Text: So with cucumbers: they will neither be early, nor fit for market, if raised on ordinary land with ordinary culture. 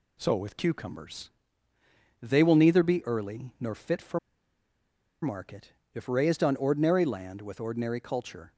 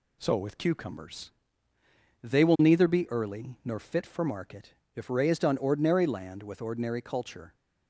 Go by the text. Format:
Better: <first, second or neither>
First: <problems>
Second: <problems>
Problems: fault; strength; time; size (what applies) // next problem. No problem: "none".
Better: second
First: pauses between "for" and "market"; at 4.1 s; 1.0 s long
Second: none